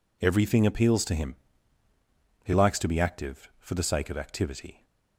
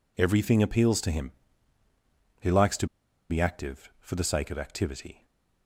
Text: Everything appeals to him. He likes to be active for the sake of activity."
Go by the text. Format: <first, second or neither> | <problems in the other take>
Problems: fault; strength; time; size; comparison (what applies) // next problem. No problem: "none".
first | pauses between "to" and "be"; at 2.8 s; 0.43 s long